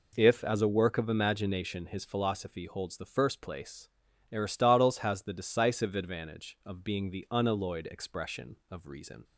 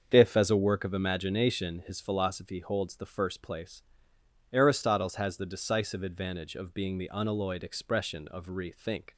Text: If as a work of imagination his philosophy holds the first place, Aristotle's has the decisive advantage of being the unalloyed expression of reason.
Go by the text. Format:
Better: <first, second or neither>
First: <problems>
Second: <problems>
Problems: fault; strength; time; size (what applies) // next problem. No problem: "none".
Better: first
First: none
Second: starts louder than the rest; until 1.1 s; 7 dB // says "rethink" for "reason"; at 8.4 s